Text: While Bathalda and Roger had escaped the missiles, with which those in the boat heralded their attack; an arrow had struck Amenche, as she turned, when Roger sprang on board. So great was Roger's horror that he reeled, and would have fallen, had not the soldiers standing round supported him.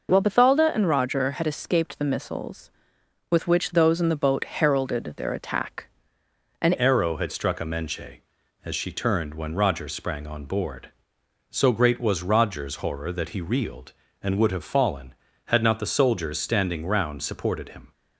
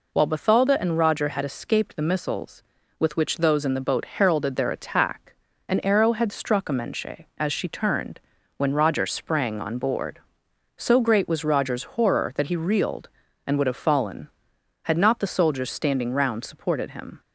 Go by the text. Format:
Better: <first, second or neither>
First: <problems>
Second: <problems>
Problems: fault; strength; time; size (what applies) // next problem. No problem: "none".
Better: second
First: changes voice at "arrow"; from 6.7 s on; 11.2 s long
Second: none